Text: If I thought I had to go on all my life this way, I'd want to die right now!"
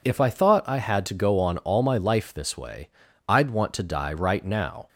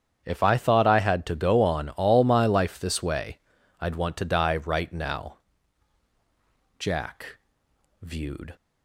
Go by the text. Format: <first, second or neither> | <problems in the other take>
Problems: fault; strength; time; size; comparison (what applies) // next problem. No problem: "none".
first | starts louder than the rest; strong; until 1.2 s; 8.5 dB // goes on to say "Jack viewed"; strong; from 6.7 s on; 1.7 s long